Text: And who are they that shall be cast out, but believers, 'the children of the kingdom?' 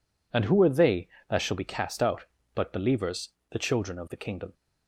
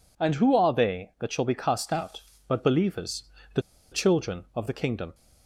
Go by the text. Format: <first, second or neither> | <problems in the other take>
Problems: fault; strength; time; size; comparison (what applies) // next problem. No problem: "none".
first | pauses between "the" and "children"; slight; at 3.6 s; 0.30 s long